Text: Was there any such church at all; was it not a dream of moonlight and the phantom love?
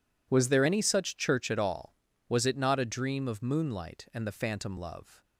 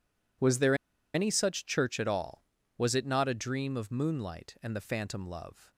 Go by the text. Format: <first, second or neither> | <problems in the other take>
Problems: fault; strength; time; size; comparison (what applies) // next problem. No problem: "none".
first | pauses between "there" and "any"; at 0.7 s; 0.39 s long